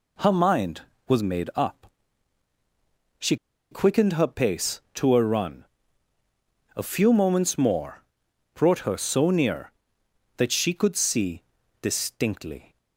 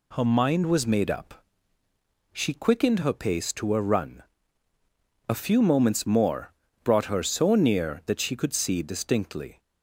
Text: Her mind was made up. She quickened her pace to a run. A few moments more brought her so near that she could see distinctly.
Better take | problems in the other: second | pauses between "She" and "quickened"; slight; at 3.3 s; 0.35 s long // pauses between "more" and "brought"; noticeable; at 8.0 s; 0.52 s long; slight in the second // pauses between "see" and "distinctly"; at 11.4 s; 0.38 s long

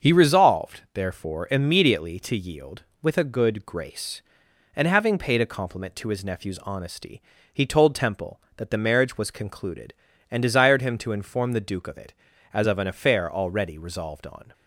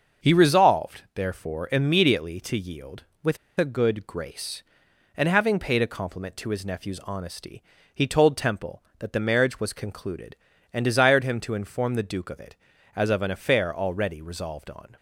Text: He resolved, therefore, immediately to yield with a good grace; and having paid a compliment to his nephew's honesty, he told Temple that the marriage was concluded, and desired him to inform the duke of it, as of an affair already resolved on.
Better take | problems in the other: first | starts louder than the rest; until 1.3 s; 6.5 dB; also in the first // pauses between "with" and "a"; slight; at 3.3 s; 0.22 s long

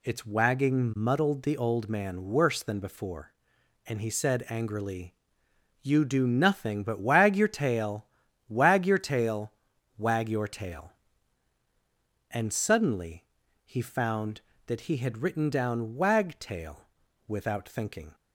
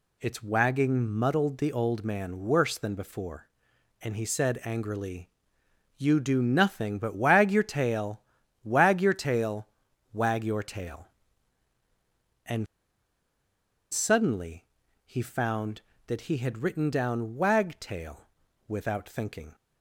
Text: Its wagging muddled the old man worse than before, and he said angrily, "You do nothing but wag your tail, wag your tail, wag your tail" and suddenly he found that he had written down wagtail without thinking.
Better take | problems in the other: first | pauses between "and" and "suddenly"; strong; at 12.6 s; 1.2 s long // pauses between "suddenly" and "he"; at 14.6 s; 0.40 s long; also in the first // pauses between "wagtail" and "without"; at 18.2 s; 0.40 s long; also in the first

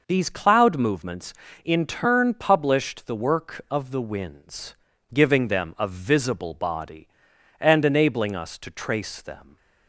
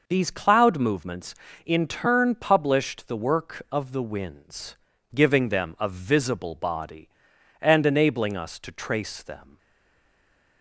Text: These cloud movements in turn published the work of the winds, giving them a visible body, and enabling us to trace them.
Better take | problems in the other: first | stays silent after the last word; from 9.5 s on; 1.1 s long

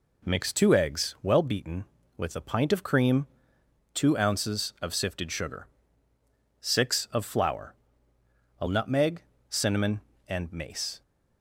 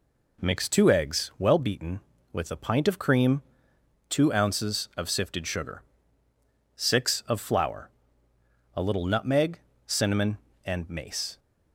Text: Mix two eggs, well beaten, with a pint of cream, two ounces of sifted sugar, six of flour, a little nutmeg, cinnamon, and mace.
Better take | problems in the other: second | skips "little"; at 8.6 s

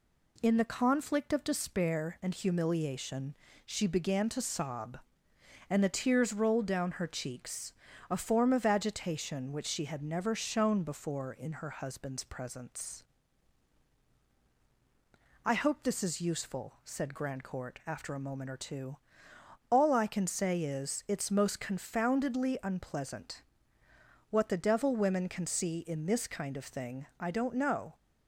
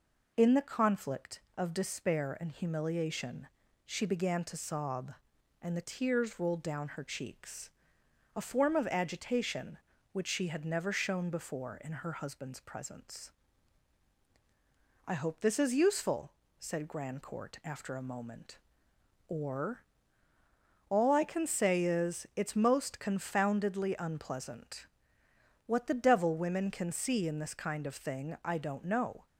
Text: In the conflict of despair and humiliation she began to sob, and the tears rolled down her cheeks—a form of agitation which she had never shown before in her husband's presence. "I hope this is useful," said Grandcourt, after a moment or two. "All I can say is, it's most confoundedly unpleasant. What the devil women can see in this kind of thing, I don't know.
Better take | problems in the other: first | pauses between "humiliation" and "she"; at 3.4 s; 0.40 s long; slight in the first // skips "two"; at 20.3 s

